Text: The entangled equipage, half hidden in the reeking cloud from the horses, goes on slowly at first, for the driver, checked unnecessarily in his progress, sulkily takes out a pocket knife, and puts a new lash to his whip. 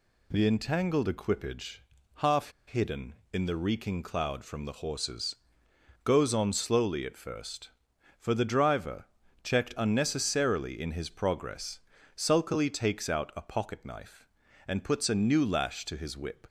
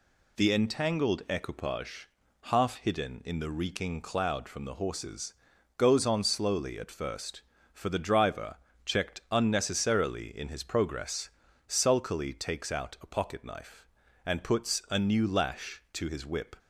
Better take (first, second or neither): second